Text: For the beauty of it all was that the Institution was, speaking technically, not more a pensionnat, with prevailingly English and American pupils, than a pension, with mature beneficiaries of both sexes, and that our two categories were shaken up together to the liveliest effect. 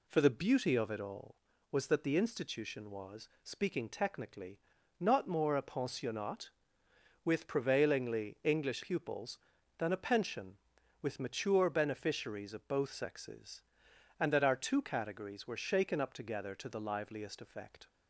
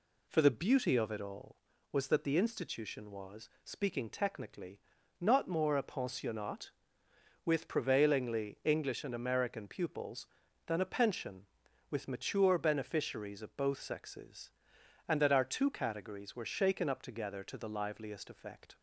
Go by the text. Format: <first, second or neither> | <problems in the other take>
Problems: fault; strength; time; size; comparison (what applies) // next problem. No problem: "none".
second | skips "and American"; at 8.8 s